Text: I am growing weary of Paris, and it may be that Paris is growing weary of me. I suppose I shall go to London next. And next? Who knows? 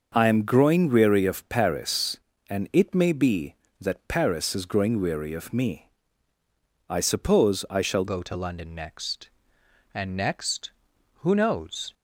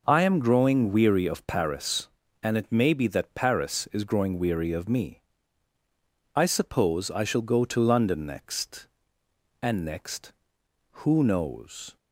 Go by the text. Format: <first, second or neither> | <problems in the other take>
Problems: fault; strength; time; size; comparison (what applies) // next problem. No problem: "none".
second | starts louder than the rest; until 1.1 s; 6.5 dB // changes voice at "go"; from 8.0 s on; 3.9 s long